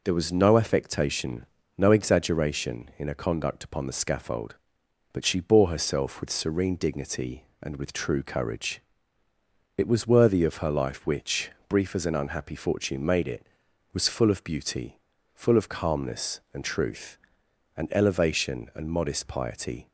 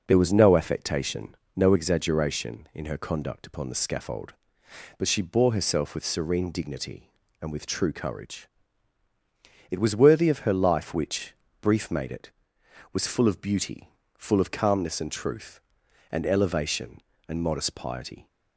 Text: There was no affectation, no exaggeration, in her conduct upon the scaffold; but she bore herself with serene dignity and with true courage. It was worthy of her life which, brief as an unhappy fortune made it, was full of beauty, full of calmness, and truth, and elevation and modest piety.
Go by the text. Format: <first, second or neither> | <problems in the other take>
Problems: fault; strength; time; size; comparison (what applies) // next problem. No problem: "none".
first | skips "as an unhappy fortune"; at 11.8 s